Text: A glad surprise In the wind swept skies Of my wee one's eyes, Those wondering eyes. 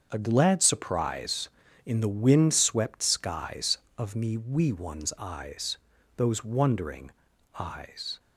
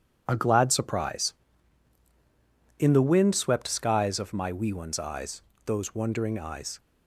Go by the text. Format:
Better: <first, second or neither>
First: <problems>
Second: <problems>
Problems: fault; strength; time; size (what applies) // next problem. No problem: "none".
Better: second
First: starts louder than the rest; until 1.1 s; 7 dB // says "me" for "my"; at 4.1 s // pauses between "wondering" and "eyes"; noticeable; at 7.1 s; 0.46 s long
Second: none